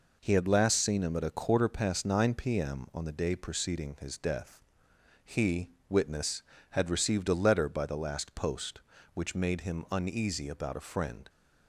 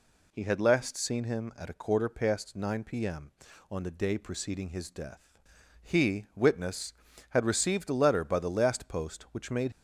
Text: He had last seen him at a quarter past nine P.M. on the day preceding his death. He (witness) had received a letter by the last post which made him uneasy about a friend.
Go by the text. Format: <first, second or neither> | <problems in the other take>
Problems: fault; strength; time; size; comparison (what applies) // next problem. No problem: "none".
first | stops before "him uneasy about a friend"; at 9.7 s